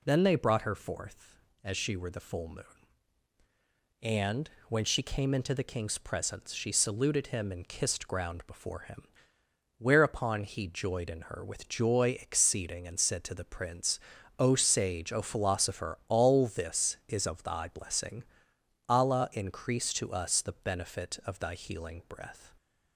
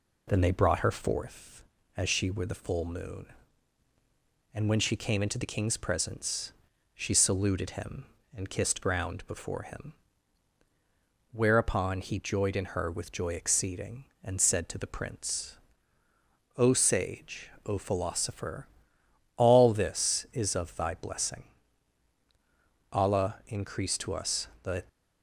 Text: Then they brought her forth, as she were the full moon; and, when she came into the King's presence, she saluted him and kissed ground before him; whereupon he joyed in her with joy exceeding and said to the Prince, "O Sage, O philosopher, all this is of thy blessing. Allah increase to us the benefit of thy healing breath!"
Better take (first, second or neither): first